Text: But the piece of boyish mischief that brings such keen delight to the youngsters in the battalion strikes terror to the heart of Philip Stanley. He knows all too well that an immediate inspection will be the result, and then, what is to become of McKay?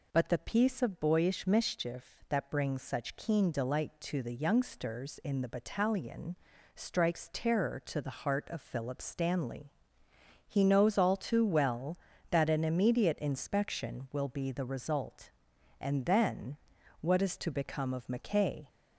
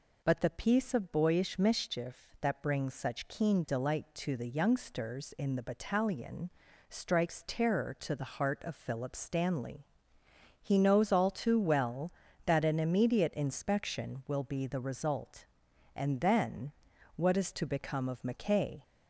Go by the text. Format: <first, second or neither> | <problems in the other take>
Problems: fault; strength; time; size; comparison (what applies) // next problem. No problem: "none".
neither | pauses between "battalion" and "strikes"; the same in both